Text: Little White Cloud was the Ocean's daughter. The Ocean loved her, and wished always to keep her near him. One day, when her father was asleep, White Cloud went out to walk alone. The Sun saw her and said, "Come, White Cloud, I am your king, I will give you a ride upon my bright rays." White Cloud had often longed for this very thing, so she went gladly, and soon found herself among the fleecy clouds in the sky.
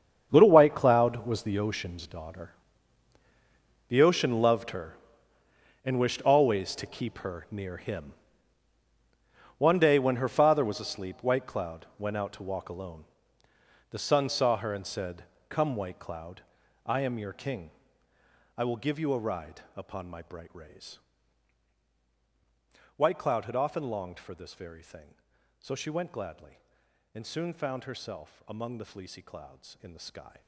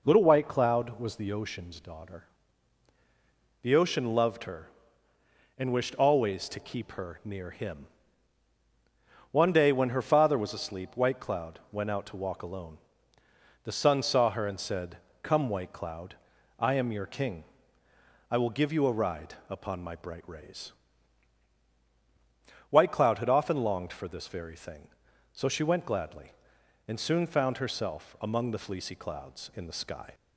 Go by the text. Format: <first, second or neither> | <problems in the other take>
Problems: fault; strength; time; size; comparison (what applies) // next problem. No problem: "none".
second | gets quieter; strong; throughout; 15 dB